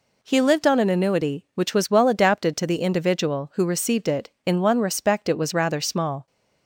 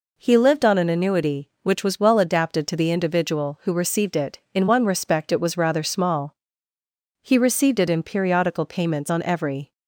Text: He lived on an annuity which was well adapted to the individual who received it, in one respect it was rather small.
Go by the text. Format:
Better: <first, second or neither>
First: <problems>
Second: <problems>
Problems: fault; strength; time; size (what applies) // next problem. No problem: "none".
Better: first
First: none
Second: goes on to say "He received it in periodical payments on every"; strong; from 7.2 s on; 2.5 s long